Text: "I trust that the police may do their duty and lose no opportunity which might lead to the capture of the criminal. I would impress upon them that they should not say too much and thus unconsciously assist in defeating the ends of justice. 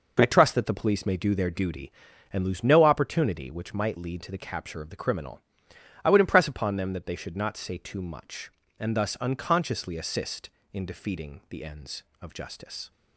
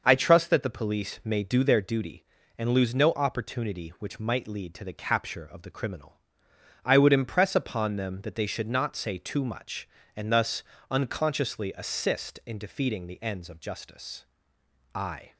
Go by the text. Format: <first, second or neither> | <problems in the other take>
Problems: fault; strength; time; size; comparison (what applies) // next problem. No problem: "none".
first | starts louder than the rest; noticeable; until 1.0 s; 6 dB // pauses between "thus" and "unconsciously"; slight; at 10.6 s; 0.30 s long // goes on to say "I"; slight; from 14.9 s on; 0.40 s long